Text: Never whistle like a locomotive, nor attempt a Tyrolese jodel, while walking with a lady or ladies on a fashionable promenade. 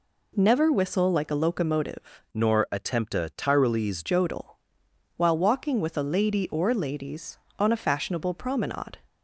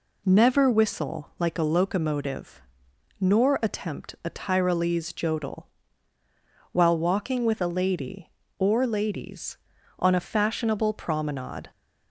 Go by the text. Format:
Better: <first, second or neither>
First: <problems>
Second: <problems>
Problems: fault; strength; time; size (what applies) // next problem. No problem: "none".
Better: second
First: changes voice from "nor" to "Tyrolese"; from 2.3 to 4.0 s; 1.7 s long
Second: none